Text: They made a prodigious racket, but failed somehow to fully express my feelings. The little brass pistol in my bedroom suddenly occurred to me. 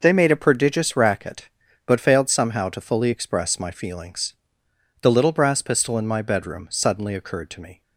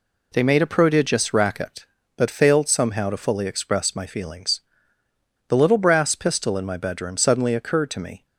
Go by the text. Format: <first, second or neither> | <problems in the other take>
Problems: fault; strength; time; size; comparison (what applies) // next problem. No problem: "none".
neither | none